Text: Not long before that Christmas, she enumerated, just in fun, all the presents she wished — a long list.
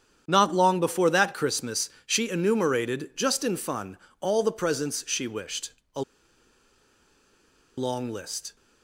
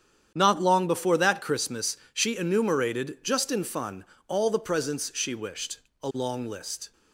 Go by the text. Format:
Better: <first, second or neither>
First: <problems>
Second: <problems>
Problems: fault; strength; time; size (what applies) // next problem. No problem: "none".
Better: second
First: starts louder than the rest; strong; until 1.2 s; 9 dB // pauses between "a" and "long"; strong; at 6.0 s; 1.7 s long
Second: starts louder than the rest; strong; until 1.3 s; 9 dB